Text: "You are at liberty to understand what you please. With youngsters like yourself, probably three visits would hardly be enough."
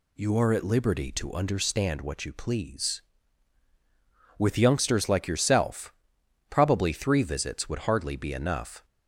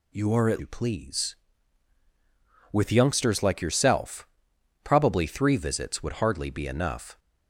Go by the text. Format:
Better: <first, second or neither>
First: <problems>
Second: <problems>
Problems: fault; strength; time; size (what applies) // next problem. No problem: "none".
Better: first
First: none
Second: skips "liberty to understand what"; at 0.5 s